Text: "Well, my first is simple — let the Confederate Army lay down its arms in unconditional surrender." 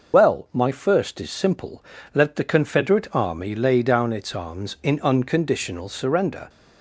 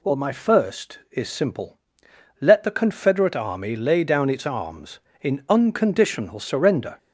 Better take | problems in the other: second | loses the start of "Well"; at 0.1 s; 50 ms

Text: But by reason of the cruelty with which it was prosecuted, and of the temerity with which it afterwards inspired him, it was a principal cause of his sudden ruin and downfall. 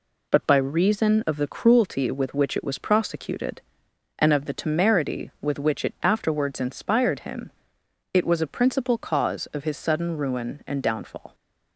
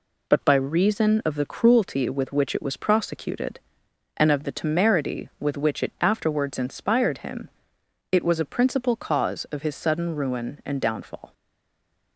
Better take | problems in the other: first | stays silent after the last word; slight; from 11.3 s on; 0.8 s long

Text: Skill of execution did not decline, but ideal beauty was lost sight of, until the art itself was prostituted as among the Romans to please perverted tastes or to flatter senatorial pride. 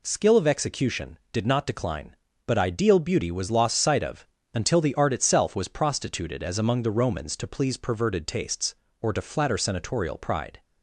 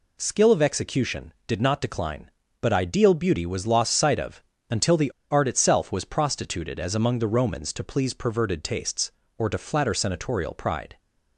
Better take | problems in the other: first | pauses between "the" and "art"; slight; at 5.1 s; 0.19 s long

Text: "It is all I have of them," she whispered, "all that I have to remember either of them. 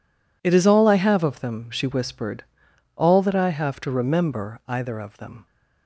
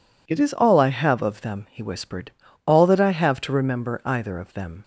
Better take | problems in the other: first | says "he" for "she"; at 1.7 s

